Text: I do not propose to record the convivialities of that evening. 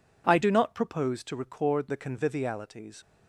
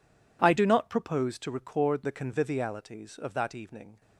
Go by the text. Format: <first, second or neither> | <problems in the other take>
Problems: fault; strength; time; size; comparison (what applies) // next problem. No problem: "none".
second | stops before "of that evening"; at 3.0 s